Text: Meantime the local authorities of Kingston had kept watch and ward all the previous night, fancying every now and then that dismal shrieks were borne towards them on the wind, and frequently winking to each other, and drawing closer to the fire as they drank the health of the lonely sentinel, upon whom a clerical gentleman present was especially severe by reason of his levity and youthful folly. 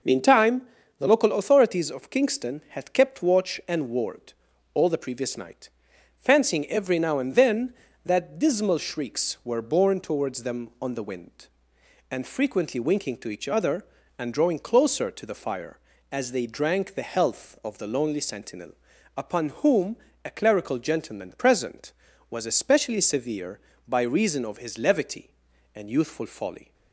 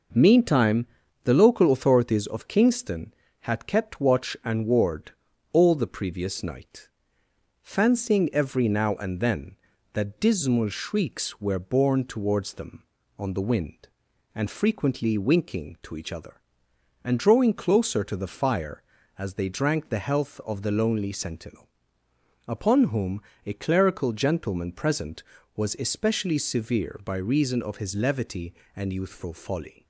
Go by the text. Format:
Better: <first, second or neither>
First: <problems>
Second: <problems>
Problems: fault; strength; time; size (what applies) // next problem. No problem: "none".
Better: neither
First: pauses between "Meantime" and "the"; slight; at 0.6 s; 0.36 s long // pauses between "ward" and "all"; at 4.3 s; 0.40 s long // pauses between "whom" and "a"; slight; at 19.9 s; 0.30 s long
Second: pauses between "Meantime" and "the"; at 0.8 s; 0.38 s long // pauses between "ward" and "all"; at 5.1 s; 0.42 s long // pauses between "whom" and "a"; slight; at 23.2 s; 0.24 s long